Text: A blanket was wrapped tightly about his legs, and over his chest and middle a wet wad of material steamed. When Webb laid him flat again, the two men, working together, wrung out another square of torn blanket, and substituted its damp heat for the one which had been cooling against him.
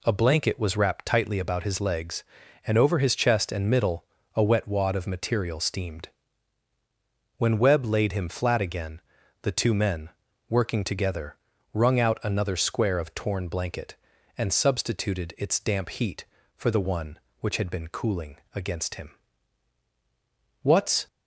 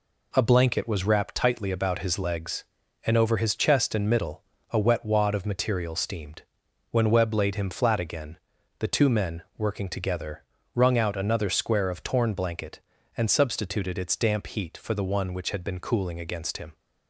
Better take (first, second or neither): second